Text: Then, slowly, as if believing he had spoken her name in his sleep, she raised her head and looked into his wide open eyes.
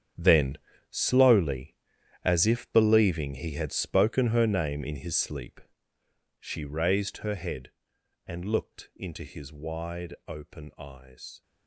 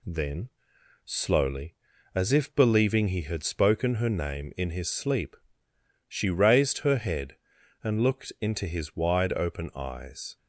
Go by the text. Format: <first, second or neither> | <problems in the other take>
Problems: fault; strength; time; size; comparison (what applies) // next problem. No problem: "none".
second | gets quieter; strong; throughout; 13.5 dB